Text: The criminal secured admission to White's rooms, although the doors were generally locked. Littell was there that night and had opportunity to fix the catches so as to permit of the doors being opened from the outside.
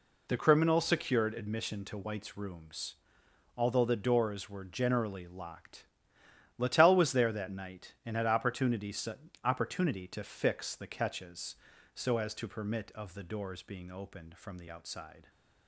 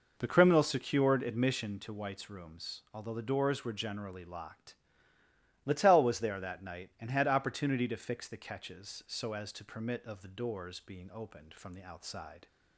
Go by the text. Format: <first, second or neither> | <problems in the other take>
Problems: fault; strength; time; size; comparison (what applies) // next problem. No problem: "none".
second | says "opportunity" twice; at 9.4 s